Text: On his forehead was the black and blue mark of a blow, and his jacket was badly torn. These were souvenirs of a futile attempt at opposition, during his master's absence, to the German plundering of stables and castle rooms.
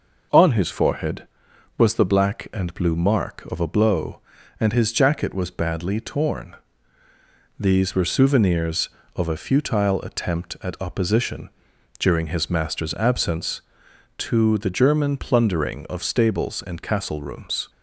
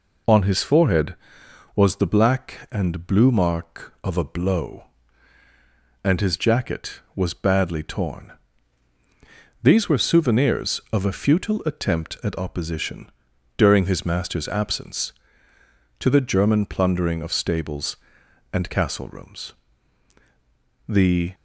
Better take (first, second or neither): first